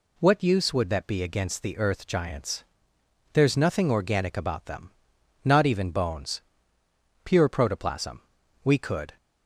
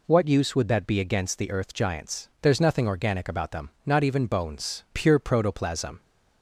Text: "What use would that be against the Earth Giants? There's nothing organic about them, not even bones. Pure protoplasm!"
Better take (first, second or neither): second